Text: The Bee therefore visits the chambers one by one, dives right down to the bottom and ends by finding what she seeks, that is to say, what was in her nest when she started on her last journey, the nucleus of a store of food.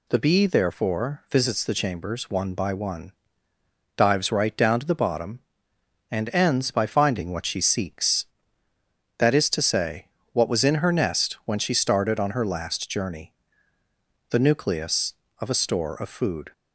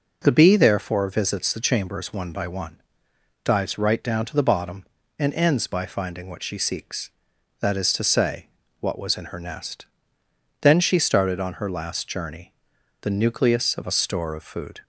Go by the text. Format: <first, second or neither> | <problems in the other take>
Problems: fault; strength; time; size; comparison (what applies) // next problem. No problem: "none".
first | says "then" for "when"; at 10.6 s